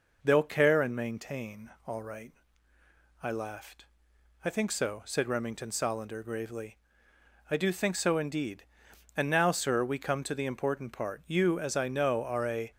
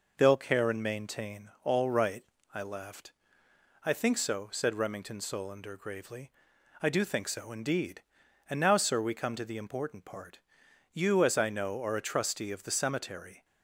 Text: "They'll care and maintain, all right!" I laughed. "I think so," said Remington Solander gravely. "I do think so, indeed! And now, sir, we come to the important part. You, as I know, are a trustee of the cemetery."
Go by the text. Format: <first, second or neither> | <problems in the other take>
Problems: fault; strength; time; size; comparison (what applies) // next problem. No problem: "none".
second | stops before "trustee of the cemetery"; at 12.7 s